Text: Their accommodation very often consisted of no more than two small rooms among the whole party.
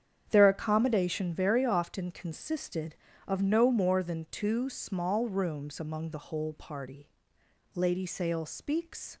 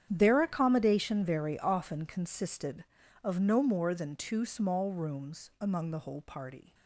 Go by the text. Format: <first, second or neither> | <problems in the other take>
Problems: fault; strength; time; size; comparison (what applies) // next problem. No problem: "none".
second | starts louder than the rest; strong; until 1.3 s; 8.5 dB; strong in the second // goes on to say "Lady Sale speaks"; from 7.7 s on; 1.4 s long